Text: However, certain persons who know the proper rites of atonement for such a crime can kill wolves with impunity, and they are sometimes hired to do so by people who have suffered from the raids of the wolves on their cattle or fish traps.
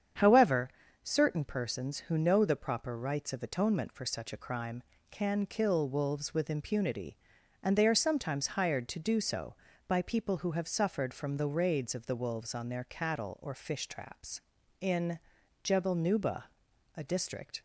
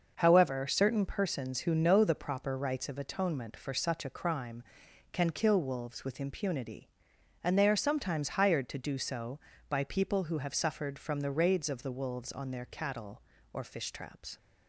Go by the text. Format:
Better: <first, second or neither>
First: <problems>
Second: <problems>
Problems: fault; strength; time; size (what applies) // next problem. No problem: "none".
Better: second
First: starts louder than the rest; strong; until 1.4 s; 8 dB // goes on to say "In Jebel Nuba a district"; strong; from 14.8 s on; 2.8 s long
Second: starts louder than the rest; noticeable; until 1.1 s; 6 dB